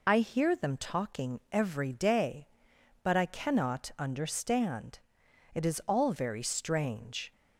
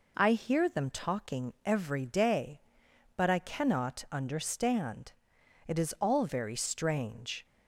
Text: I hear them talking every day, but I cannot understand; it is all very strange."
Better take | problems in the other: second | loses the start of "I"; at 0.0 s; 35 ms

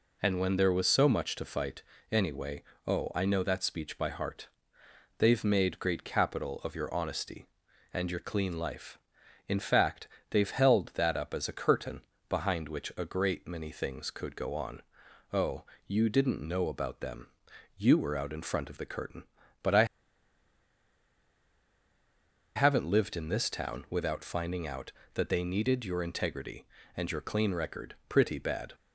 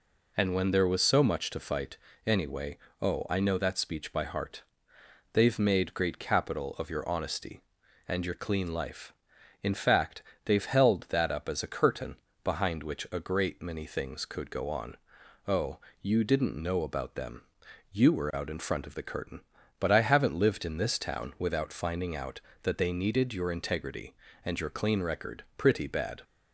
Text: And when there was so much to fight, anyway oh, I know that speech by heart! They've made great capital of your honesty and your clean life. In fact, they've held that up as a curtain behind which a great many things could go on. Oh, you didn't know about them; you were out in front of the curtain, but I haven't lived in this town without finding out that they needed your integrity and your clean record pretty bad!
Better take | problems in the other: second | pauses between "anyway" and "oh"; slight; at 2.6 s; 0.24 s long; slight in the second // pauses between "curtain" and "behind"; slight; at 12.0 s; 0.28 s long; slight in the second // pauses between "I" and "haven't"; strong; at 19.8 s; 2.7 s long

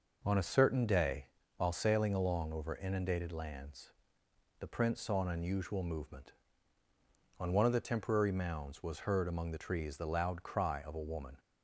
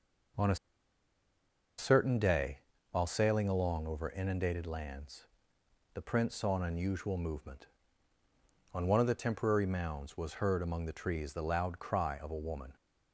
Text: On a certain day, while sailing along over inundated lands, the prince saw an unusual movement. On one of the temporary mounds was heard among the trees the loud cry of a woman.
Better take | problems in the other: first | pauses between "a" and "certain"; at 0.5 s; 1.2 s long

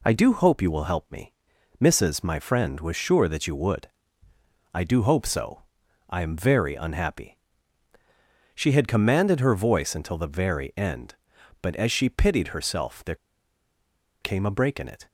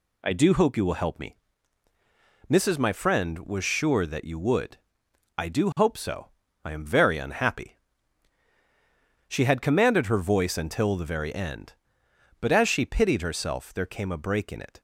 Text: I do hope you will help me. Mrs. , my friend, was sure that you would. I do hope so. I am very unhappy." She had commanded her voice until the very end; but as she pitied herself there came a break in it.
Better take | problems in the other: second | pauses between "there" and "came"; at 13.1 s; 1.0 s long

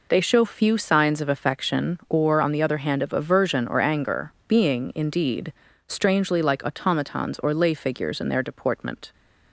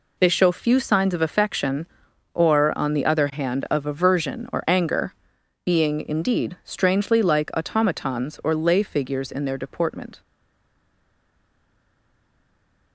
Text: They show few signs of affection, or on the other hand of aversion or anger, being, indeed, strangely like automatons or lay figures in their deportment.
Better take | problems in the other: first | stays silent after the last word; strong; from 10.2 s on; 2.7 s long

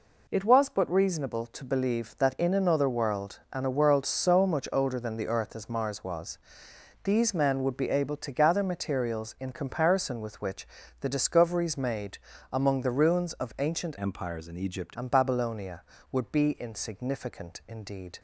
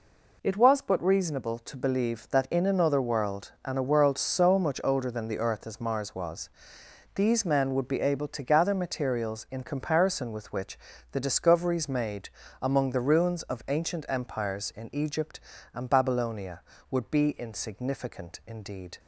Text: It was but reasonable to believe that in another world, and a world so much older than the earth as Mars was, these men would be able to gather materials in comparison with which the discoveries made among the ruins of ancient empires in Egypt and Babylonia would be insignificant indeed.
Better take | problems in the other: second | pauses between "which" and "the"; slight; at 10.6 s; 0.32 s long; slight in the second // pauses between "made" and "among"; slight; at 12.1 s; 0.34 s long; slight in the second // changes voice from "empires" to "Egypt"; from 13.9 to 14.9 s; 1.0 s long

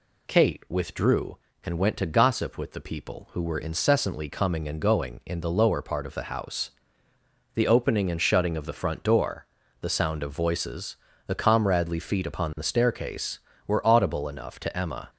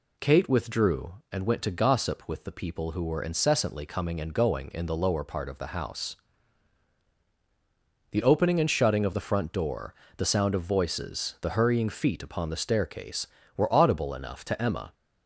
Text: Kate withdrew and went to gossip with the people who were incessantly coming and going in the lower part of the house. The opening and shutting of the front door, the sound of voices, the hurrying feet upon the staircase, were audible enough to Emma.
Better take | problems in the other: second | says "comradely" for "hurrying"; at 11.3 s

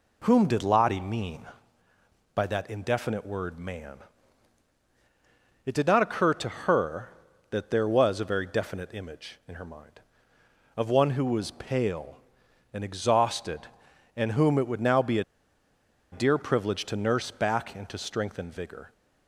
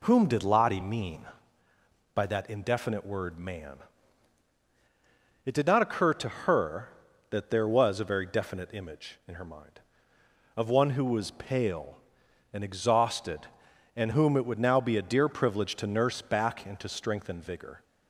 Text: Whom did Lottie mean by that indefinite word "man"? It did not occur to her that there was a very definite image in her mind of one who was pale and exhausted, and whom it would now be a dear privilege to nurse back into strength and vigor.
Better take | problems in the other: second | pauses between "a" and "dear"; noticeable; at 15.2 s; 0.88 s long

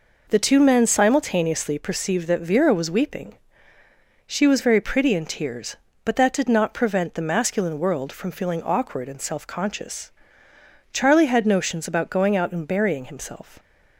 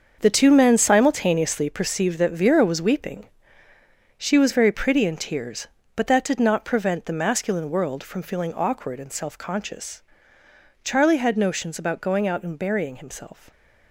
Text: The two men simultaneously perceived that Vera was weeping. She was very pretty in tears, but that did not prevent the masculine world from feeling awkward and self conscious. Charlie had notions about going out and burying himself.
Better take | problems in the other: first | gets quieter; strong; throughout; 11 dB

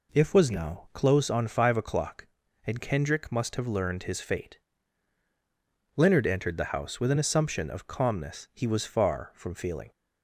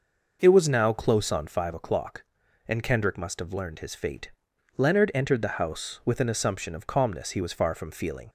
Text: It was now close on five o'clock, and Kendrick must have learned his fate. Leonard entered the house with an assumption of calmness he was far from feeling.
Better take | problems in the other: second | says "If" for "It"; at 0.1 s

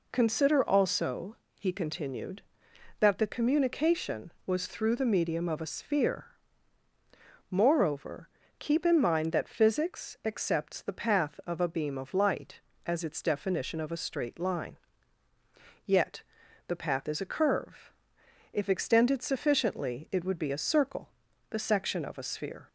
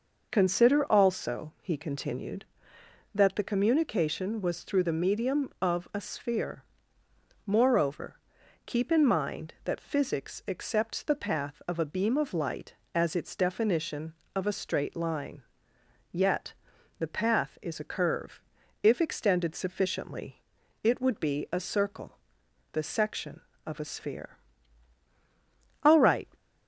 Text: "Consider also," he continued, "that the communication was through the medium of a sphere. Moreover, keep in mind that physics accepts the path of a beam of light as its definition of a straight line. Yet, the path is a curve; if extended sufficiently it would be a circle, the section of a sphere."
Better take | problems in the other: first | pauses between "sufficiently" and "it"; at 20.4 s; 0.40 s long // goes on to say "All right"; slight; from 25.8 s on; 0.48 s long

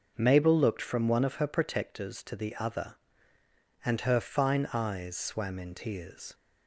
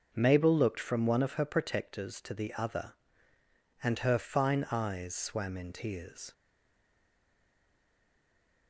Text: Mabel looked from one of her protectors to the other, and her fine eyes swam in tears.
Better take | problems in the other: first | stays silent after the last word; from 6.3 s on; 2.3 s long

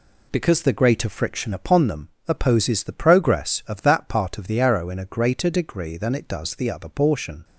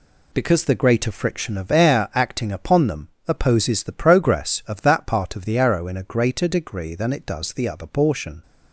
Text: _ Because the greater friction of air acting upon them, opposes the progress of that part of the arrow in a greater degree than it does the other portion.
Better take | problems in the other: second | skips "of air acting"; at 1.5 s

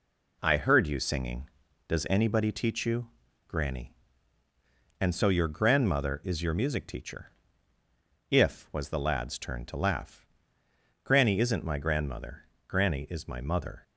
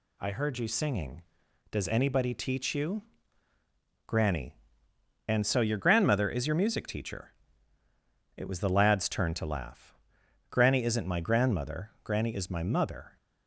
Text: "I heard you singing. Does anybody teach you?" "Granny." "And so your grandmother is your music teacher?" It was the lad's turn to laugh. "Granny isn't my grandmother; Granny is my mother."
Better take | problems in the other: second | says "If" for "It"; at 8.3 s

